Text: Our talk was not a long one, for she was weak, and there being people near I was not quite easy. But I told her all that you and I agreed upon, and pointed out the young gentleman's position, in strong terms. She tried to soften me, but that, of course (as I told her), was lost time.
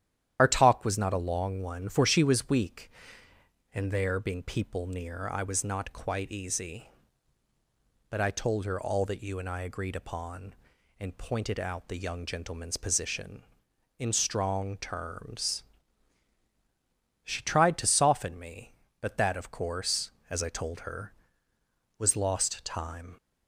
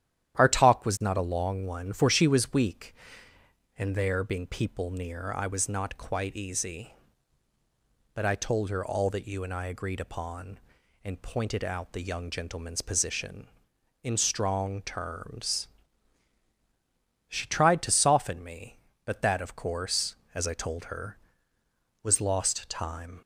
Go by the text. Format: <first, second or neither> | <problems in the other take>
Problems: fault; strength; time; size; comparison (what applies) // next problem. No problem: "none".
second | loses the start of "Our"; at 0.3 s; 55 ms // starts louder than the rest; strong; until 1.4 s; 10.5 dB; strong in the second